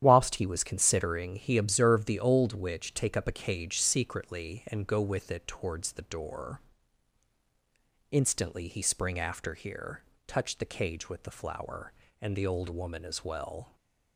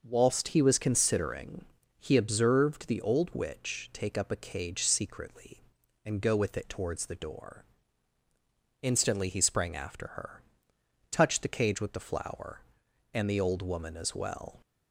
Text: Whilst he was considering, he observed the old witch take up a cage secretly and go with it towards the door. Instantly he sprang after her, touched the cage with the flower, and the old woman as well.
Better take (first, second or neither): second